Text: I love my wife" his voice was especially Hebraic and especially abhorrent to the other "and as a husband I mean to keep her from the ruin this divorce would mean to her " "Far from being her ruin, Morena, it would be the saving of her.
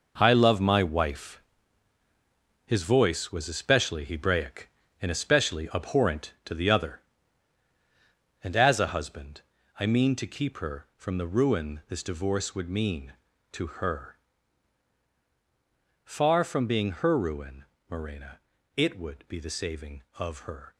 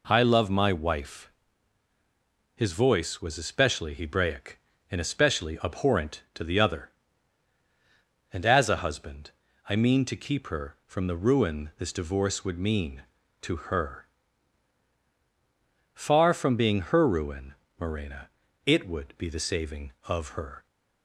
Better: second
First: gets quieter; strong; throughout; 15.5 dB // pauses between "wife" and "his"; at 1.4 s; 1.2 s long // pauses between "husband" and "I"; slight; at 9.4 s; 0.36 s long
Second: pauses between "wife" and "his"; at 1.3 s; 1.2 s long // pauses between "husband" and "I"; slight; at 9.3 s; 0.36 s long

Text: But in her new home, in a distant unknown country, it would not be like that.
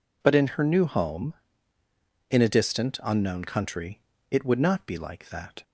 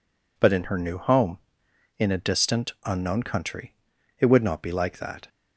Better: neither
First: none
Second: none

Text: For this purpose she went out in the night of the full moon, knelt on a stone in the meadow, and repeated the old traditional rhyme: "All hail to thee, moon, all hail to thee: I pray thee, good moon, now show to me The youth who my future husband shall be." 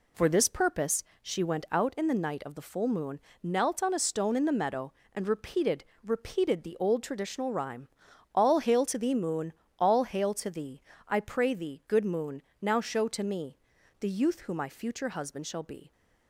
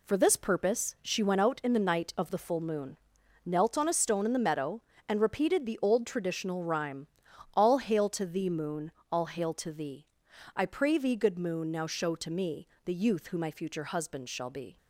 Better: second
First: pauses between "purpose" and "she"; slight; at 1.0 s; 0.18 s long // says "repeated" twice; at 6.0 s // pauses between "me" and "The"; at 13.5 s; 0.42 s long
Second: pauses between "me" and "The"; slight; at 12.6 s; 0.16 s long

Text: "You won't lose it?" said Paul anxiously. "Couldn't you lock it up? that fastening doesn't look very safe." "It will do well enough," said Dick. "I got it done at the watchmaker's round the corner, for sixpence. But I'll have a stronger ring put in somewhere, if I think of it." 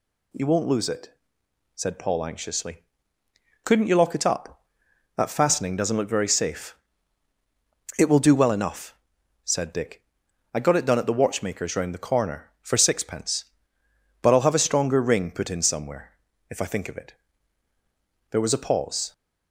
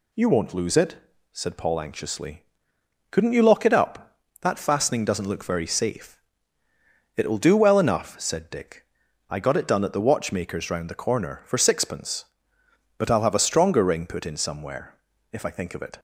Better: second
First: goes on to say "There was a pause"; noticeable; from 18.3 s on; 0.82 s long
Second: none

